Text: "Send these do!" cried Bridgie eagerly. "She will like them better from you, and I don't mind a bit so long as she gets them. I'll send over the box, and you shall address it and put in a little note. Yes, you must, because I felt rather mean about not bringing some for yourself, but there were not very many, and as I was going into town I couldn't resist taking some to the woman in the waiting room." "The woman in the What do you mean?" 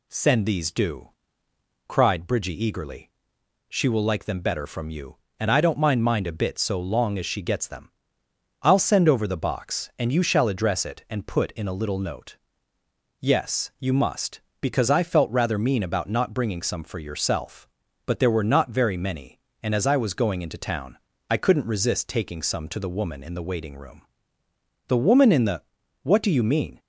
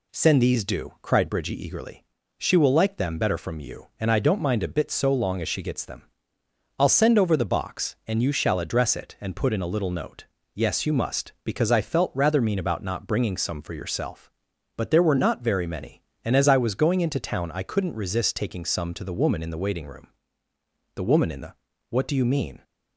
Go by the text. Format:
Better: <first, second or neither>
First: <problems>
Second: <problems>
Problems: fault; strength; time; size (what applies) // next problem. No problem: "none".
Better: second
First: says "mind" twice; at 6.0 s // pauses between "town" and "I"; slight; at 20.9 s; 0.32 s long // pauses between "the" and "What"; at 25.6 s; 0.40 s long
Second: pauses between "the" and "What"; at 21.5 s; 0.38 s long